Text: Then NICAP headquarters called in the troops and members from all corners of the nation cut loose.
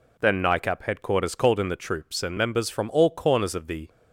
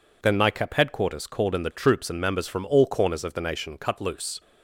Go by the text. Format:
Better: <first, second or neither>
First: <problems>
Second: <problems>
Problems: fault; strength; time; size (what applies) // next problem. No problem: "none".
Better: second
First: stops before "nation cut loose"; at 3.8 s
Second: none